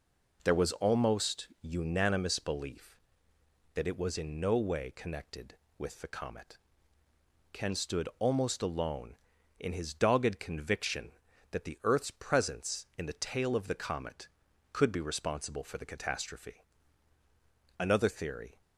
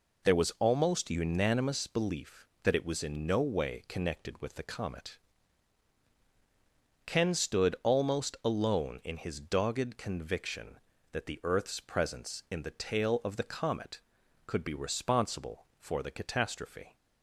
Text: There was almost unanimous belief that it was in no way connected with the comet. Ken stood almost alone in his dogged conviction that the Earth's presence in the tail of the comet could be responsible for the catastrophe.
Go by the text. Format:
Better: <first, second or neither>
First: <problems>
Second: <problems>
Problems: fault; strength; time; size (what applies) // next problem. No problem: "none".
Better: second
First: goes on to say "Another theory"; noticeable; from 17.7 s on; 0.82 s long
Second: none